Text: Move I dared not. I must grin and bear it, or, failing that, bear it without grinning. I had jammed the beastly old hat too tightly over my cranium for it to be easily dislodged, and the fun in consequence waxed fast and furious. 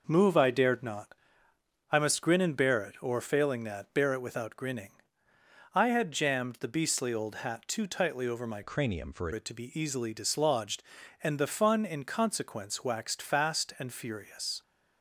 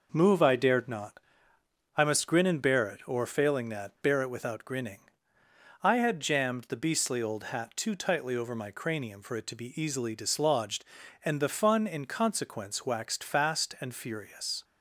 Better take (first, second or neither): second